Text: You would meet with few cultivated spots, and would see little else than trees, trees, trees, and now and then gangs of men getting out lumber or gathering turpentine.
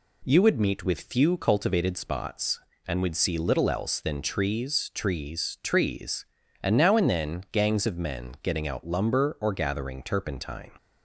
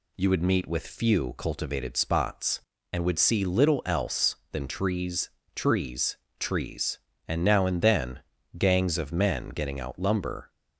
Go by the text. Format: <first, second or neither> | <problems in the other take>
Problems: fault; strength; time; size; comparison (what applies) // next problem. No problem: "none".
first | pauses between "then" and "gangs"; at 8.1 s; 0.38 s long // stops before "or gathering turpentine"; at 10.4 s